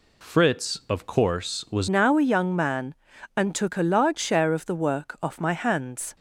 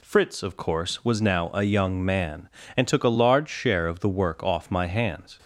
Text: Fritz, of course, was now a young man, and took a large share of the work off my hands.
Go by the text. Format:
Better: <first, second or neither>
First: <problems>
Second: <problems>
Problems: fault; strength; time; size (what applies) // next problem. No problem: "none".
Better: second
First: changes voice at "now"; from 1.8 s on; 4.3 s long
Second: none